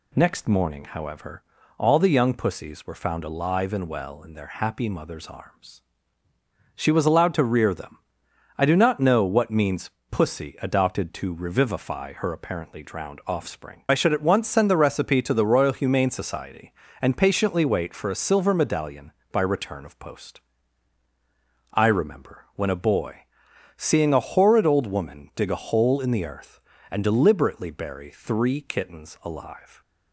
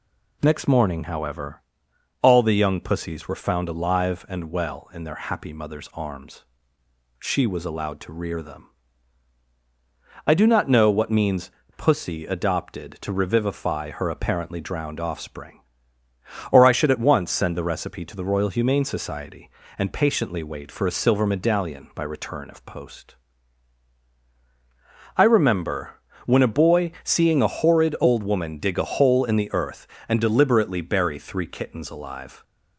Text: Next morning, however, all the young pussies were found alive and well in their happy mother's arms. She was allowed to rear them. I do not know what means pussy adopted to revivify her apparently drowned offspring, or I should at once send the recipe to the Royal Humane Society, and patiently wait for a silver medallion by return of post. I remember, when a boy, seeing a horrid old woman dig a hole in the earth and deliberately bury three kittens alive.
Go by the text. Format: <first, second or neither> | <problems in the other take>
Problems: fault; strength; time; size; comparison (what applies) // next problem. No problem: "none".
second | pauses between "means" and "pussy"; slight; at 9.8 s; 0.22 s long; slight in the second // skips "or"; at 13.8 s